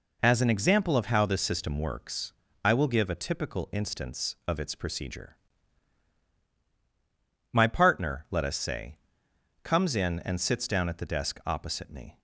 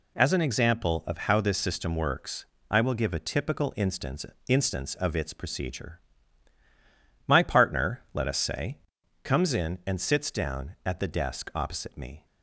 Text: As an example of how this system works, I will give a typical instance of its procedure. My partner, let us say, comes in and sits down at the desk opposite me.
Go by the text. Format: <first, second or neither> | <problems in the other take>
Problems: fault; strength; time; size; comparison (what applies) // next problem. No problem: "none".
first | says "instance" twice; at 4.4 s